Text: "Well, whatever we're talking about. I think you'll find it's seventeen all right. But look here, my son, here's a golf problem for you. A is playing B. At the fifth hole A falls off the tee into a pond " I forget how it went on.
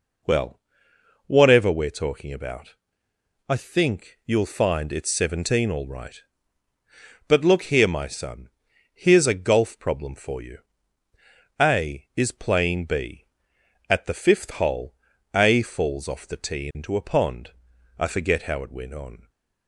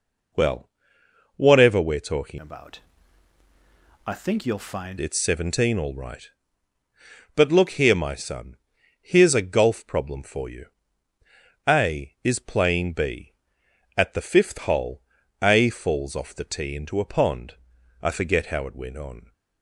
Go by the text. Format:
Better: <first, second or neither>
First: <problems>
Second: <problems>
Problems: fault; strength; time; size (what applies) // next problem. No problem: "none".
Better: first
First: pauses between "hole" and "A"; at 14.9 s; 0.40 s long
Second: changes voice from "about" to "find"; from 2.3 to 4.9 s; 2.6 s long // pauses between "hole" and "A"; at 15.0 s; 0.40 s long